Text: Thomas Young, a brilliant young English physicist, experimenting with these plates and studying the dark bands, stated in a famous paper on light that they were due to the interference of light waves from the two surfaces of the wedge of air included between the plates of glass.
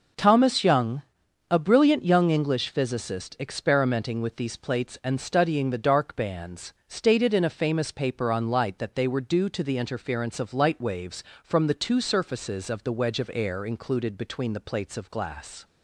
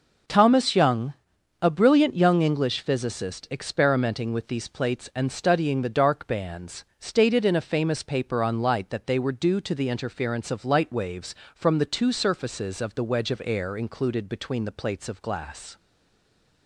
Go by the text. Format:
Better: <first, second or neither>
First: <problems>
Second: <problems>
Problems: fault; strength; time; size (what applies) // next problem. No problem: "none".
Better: first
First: none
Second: stays silent after the last word; slight; from 15.7 s on; 0.9 s long